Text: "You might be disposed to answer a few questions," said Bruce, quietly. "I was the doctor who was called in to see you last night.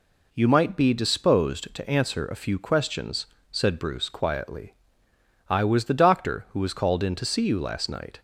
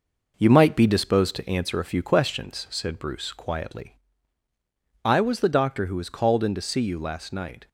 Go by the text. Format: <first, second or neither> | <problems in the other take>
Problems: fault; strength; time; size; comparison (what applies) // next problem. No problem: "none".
first | gets quieter; noticeable; throughout; 4 dB